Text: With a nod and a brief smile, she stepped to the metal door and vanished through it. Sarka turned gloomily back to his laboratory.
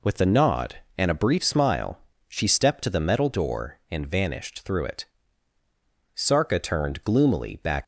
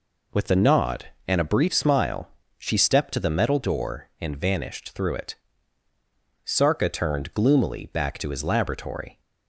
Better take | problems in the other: second | stops before "to his laboratory"; at 7.8 s

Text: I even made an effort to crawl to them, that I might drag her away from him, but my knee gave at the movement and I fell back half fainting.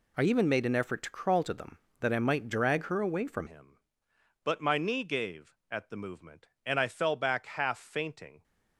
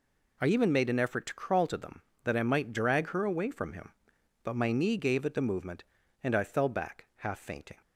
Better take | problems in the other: second | changes voice at "him"; from 3.4 s on; 5.0 s long

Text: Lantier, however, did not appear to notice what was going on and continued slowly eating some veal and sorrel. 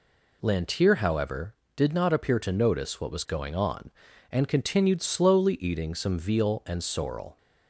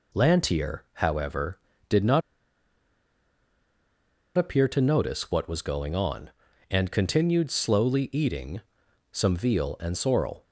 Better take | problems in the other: first | pauses between "not" and "appear"; strong; at 2.2 s; 2.1 s long // pauses between "eating" and "some"; noticeable; at 8.6 s; 0.50 s long

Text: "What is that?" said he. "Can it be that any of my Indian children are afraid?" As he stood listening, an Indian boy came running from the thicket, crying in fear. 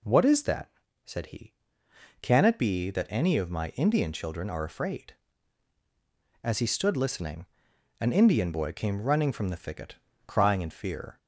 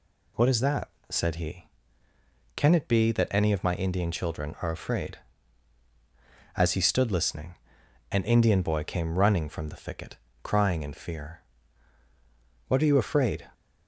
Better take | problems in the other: first | goes on to say "What are you afraid"; noticeable; from 12.6 s on; 0.80 s long

